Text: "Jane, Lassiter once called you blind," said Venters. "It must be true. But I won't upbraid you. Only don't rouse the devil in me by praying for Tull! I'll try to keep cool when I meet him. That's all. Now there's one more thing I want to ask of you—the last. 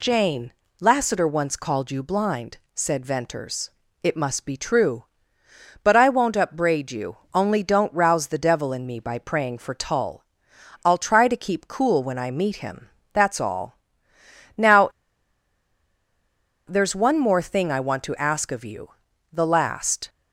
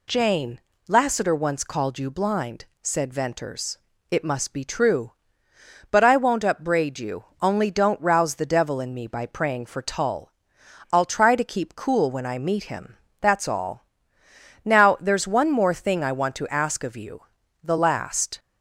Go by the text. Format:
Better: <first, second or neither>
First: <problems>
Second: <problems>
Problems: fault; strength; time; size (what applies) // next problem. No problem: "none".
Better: second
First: pauses between "Now" and "there's"; strong; at 14.8 s; 1.7 s long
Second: none